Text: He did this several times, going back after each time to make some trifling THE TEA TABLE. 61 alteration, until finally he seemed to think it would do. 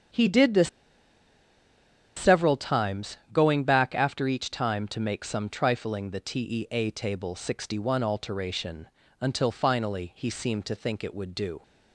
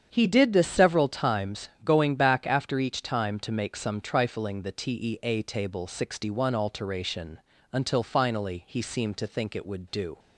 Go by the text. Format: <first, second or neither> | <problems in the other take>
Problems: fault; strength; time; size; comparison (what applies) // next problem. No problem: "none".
second | starts louder than the rest; strong; until 2.6 s; 8 dB; strong in the second // pauses between "this" and "several"; strong; at 0.6 s; 1.4 s long